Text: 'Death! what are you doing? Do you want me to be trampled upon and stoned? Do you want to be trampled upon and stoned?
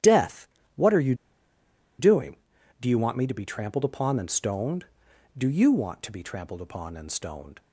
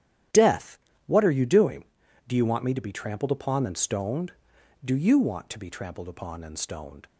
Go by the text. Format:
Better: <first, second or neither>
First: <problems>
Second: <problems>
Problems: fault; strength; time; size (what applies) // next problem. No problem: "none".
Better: second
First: starts louder than the rest; strong; until 2.1 s; 11 dB // pauses between "you" and "doing"; noticeable; at 1.1 s; 0.84 s long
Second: starts louder than the rest; strong; until 1.6 s; 11 dB